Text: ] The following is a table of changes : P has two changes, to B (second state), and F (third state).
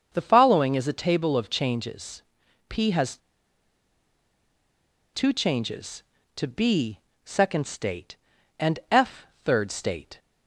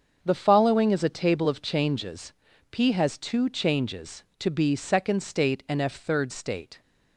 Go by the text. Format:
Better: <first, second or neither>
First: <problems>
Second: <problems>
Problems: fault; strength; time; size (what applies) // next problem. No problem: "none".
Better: second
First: starts louder than the rest; until 1.1 s; 6.5 dB // pauses between "has" and "two"; strong; at 3.1 s; 1.9 s long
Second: starts louder than the rest; until 1.2 s; 7 dB